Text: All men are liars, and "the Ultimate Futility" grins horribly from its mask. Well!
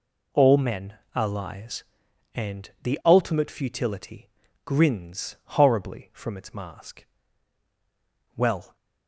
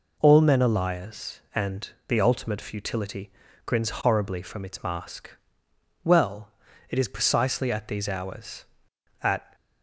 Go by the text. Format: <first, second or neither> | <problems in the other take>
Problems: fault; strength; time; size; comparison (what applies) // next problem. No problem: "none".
first | pauses between "and" and "the"; slight; at 1.8 s; 0.20 s long // pauses between "Futility" and "grins"; slight; at 3.3 s; 0.34 s long; slight in the first // goes on to say "It is precisely at these hours at"; strong; from 6.8 s on; 2.6 s long